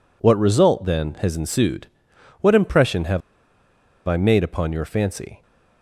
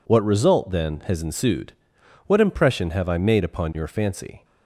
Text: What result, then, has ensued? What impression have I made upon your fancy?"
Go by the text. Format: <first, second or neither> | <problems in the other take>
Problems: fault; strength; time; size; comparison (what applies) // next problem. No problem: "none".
second | pauses between "have" and "I"; noticeable; at 3.2 s; 0.87 s long